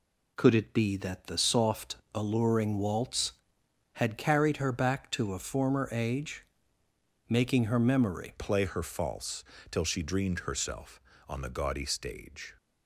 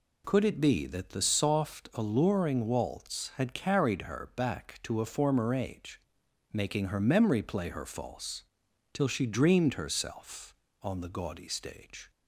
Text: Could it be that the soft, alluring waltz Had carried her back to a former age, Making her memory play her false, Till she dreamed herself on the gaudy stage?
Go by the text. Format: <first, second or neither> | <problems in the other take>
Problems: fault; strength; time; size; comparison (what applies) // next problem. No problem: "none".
second | changes voice at "play"; from 8.3 s on; 4.2 s long